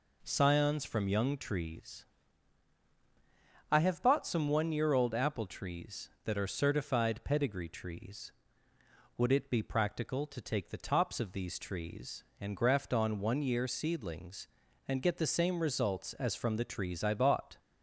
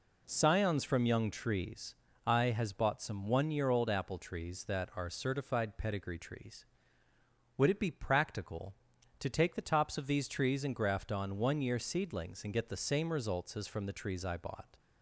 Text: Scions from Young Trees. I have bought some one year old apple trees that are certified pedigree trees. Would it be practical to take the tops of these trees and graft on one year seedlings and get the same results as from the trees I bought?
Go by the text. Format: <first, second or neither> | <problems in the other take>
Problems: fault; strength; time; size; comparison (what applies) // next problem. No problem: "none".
first | says "has" for "have"; at 2.4 s